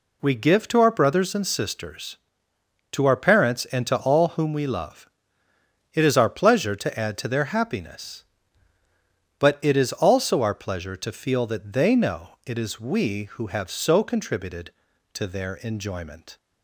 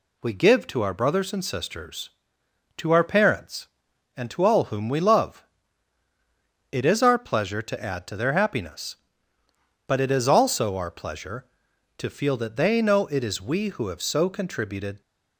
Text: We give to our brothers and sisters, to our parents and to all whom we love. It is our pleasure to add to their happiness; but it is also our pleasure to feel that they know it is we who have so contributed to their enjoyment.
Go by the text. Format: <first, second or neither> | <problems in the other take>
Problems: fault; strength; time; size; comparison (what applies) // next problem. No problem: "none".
first | stops before "to their enjoyment"; at 15.0 s